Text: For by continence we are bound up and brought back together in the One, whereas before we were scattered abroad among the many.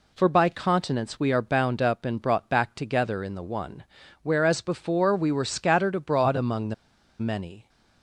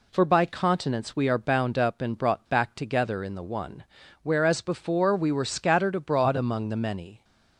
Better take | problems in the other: second | pauses between "the" and "many"; at 6.7 s; 0.45 s long

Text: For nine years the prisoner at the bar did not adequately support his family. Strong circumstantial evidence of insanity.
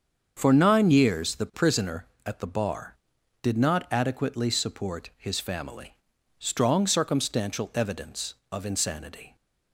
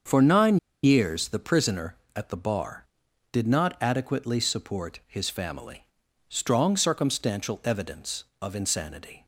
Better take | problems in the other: first | starts louder than the rest; until 1.3 s; 7 dB; also in the first // pauses between "nine" and "years"; slight; at 0.5 s; 0.25 s long

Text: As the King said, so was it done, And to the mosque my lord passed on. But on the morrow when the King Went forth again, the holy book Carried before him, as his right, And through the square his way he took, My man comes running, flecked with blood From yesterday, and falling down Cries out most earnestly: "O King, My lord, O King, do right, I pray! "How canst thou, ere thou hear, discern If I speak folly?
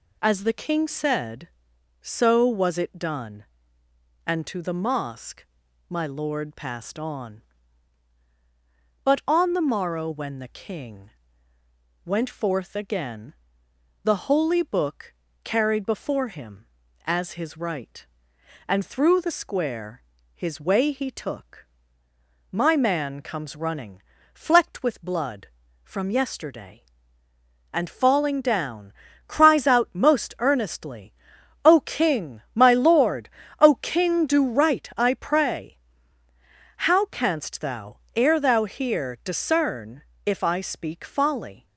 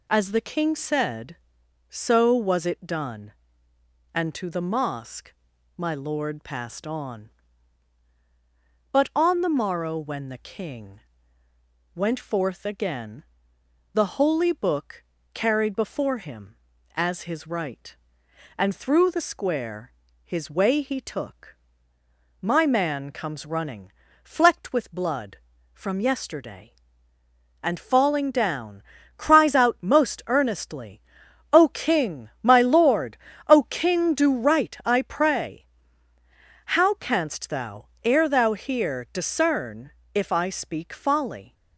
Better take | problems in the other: neither | pauses between "mosque" and "my"; the same in both // pauses between "King" and "Went"; noticeable; the same in both // pauses between "book" and "Carried"; slight; the same in both // pauses between "square" and "his"; slight; the same in both // pauses between "down" and "Cries"; slight; the same in both // pauses between "discern" and "If"; slight; the same in both

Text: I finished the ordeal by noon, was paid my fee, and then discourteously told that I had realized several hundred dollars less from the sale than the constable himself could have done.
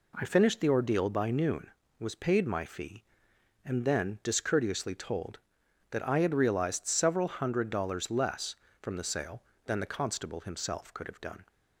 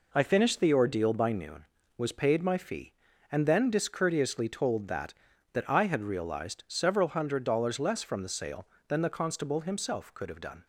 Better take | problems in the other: first | says "that" twice; at 5.5 s

